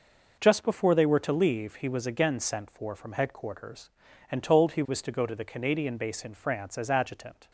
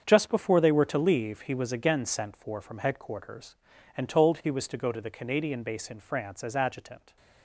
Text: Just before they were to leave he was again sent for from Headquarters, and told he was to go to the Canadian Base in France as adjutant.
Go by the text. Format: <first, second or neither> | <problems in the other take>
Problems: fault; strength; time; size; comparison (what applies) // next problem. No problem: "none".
first | gets quieter; strong; throughout; 12 dB